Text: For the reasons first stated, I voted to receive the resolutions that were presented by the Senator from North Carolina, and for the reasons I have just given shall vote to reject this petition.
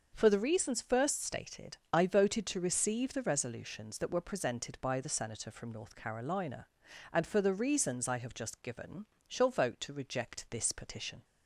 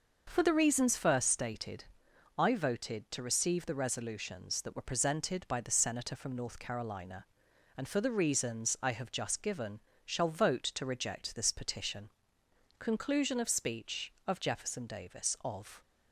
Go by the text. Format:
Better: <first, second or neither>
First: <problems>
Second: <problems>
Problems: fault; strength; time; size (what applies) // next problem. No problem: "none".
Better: first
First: starts louder than the rest; noticeable; until 1.1 s; 6 dB // pauses between "given" and "shall"; slight; at 9.0 s; 0.22 s long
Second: starts louder than the rest; noticeable; until 1.2 s; 6 dB // pauses between "given" and "shall"; slight; at 9.8 s; 0.24 s long // goes on to say "Conclusion of speech of Jefferson Davis of"; strong; from 12.7 s on; 3.0 s long